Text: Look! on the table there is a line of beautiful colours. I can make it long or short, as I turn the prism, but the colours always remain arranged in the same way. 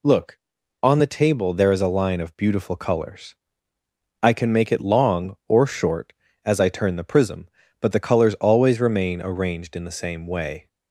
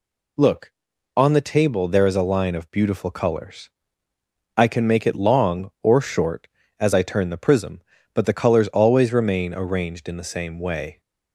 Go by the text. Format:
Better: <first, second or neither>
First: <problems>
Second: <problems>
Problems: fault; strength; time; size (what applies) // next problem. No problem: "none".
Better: neither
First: none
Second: none